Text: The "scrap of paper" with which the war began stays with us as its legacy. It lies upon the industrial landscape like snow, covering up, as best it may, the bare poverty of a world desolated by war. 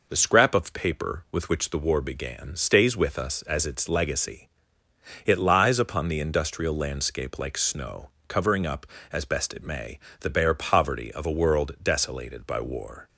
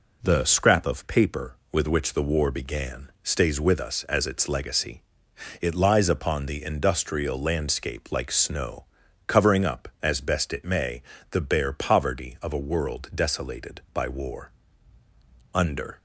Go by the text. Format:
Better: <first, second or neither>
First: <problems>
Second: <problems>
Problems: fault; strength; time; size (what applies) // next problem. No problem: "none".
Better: first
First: none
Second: goes on to say "Under"; slight; from 15.5 s on; 0.46 s long